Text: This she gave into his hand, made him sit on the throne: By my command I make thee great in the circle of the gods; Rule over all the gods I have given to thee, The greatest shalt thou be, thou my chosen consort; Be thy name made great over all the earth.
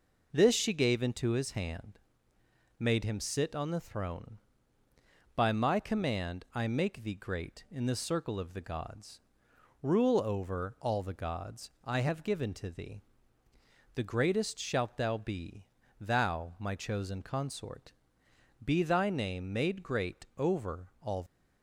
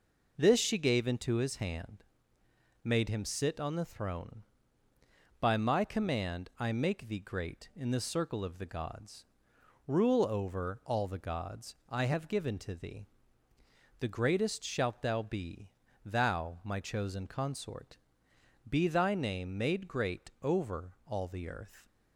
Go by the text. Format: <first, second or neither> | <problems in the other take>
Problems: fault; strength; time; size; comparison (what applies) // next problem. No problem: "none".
second | stops before "the earth"; at 21.2 s